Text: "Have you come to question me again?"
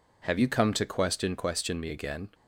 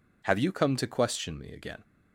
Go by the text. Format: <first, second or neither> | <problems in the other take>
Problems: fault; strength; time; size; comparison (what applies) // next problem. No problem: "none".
second | says "question" twice; at 1.3 s